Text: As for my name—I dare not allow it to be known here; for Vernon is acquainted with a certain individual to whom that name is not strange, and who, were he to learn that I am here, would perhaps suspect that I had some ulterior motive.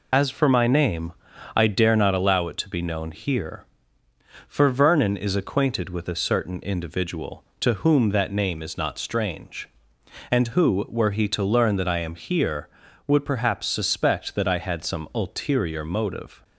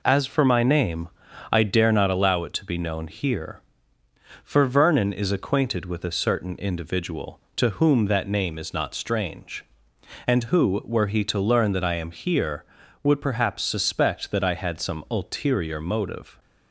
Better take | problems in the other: second | loses the start of "As"; at 0.1 s; 50 ms

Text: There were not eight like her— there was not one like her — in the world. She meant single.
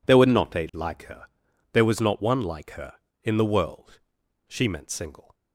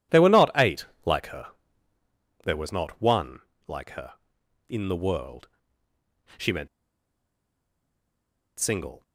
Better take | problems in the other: first | pauses between "eight" and "like"; slight; at 0.8 s; 0.18 s long // pauses between "one" and "like"; slight; at 3.4 s; 0.26 s long // pauses between "meant" and "single"; strong; at 6.6 s; 1.9 s long

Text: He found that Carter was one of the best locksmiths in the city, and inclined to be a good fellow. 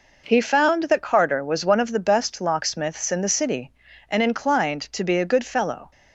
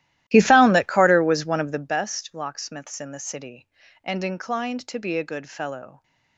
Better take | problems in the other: first | starts louder than the rest; strong; until 2.0 s; 14.5 dB

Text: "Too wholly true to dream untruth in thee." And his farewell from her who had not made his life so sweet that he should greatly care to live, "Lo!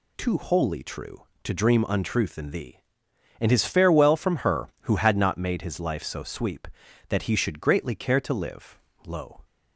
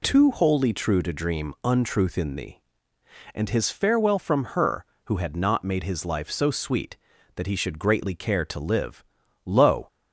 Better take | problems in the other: second | says "sweep" for "sweet"; at 6.2 s

